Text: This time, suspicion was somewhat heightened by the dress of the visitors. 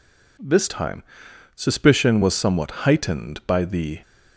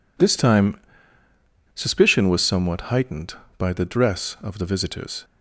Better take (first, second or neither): second